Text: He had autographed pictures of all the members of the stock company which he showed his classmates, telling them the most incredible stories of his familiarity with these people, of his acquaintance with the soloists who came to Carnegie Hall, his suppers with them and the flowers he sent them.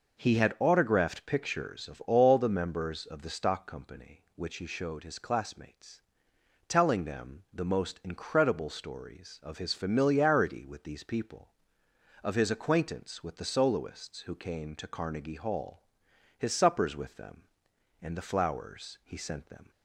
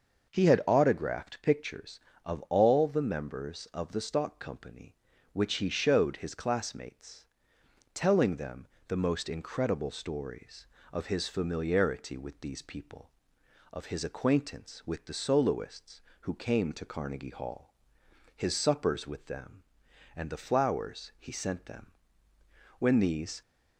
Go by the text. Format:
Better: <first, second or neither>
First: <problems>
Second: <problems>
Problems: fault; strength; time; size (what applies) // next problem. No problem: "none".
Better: first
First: none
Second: starts louder than the rest; noticeable; until 1.3 s; 6 dB // pauses between "them" and "the"; slight; at 8.6 s; 0.20 s long // goes on to say "When these"; noticeable; from 22.7 s on; 0.64 s long